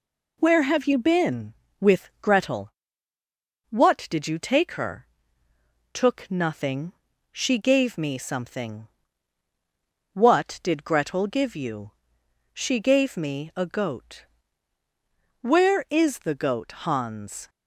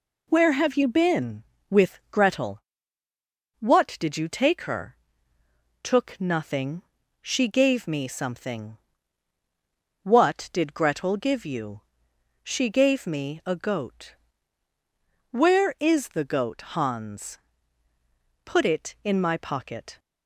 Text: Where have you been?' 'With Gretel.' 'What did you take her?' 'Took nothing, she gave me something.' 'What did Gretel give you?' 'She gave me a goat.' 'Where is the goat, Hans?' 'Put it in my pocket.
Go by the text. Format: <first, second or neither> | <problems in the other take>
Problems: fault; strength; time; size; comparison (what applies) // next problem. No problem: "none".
second | stops before "Put it in my pocket"; at 17.4 s